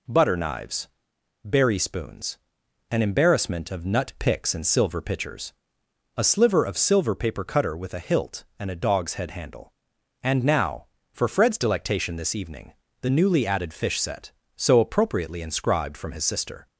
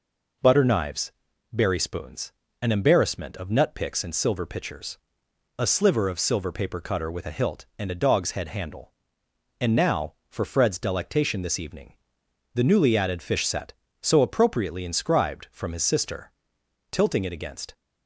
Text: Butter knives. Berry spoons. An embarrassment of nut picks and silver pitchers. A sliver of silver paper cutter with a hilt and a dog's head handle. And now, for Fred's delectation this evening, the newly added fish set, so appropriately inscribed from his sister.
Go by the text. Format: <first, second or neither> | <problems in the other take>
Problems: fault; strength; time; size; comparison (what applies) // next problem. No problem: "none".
first | goes on to say "Tilting it against"; noticeable; from 16.9 s on; 0.82 s long